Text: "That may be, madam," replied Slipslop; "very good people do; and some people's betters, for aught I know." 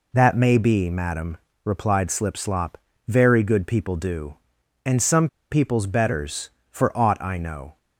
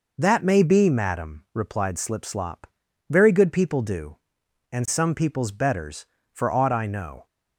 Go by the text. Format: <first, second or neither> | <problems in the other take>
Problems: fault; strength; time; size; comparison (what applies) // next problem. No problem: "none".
second | pauses between "some" and "people's"; slight; at 5.2 s; 0.23 s long